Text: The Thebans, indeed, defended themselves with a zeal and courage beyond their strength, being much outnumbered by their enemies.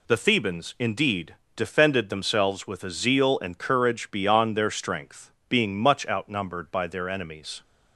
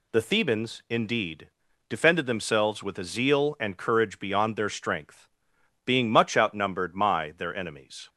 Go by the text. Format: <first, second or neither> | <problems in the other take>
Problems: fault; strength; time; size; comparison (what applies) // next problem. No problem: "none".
first | says "my" for "by"; at 6.9 s